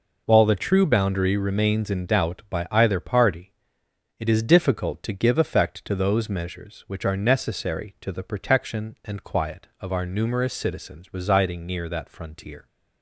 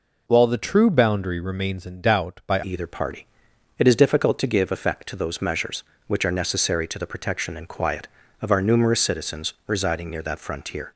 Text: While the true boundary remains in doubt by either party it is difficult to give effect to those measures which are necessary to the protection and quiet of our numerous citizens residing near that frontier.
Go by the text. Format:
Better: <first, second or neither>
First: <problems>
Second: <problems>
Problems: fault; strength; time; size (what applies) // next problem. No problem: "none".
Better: first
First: pauses between "party" and "it"; noticeable; at 3.5 s; 0.64 s long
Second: changes voice at "either"; from 2.6 s on; 8.3 s long // pauses between "party" and "it"; noticeable; at 3.2 s; 0.54 s long